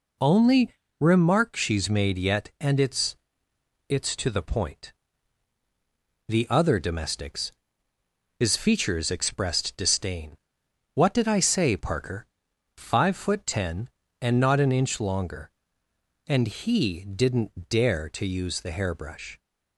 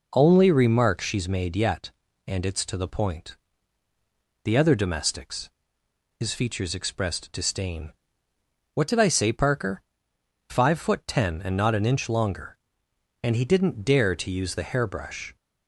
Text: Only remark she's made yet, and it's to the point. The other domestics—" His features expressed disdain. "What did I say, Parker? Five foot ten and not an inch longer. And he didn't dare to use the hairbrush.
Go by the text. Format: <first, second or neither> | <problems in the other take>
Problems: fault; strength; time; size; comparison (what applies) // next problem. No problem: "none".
second | pauses between "Only" and "remark"; slight; at 0.7 s; 0.28 s long // says "it's" twice; at 3.8 s